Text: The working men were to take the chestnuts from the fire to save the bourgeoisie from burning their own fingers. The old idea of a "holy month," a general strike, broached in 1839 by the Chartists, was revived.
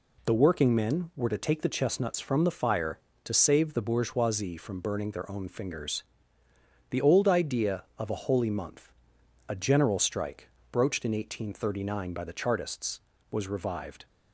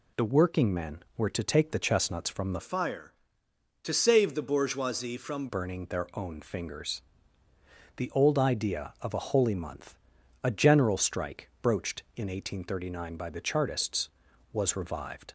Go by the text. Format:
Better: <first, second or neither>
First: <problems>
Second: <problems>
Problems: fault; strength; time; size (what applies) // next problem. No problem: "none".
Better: first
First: none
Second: changes voice from "fire" to "from"; from 2.6 to 5.4 s; 2.8 s long